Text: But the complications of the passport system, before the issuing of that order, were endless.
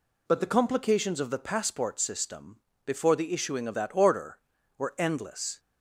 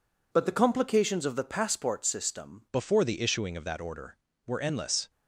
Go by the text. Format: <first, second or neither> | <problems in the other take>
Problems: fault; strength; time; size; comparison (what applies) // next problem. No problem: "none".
first | changes voice at "before"; from 2.7 s on; 2.3 s long